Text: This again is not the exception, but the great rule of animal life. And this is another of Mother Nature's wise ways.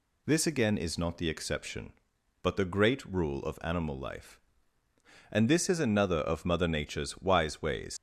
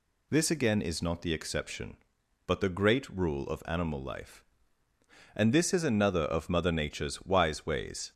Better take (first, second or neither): second